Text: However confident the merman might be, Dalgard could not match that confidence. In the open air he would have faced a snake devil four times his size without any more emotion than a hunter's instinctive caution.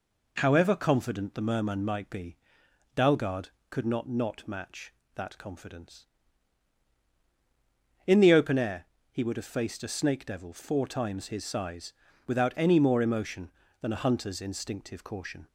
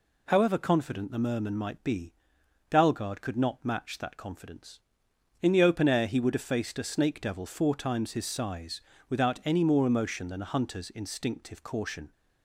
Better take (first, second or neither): second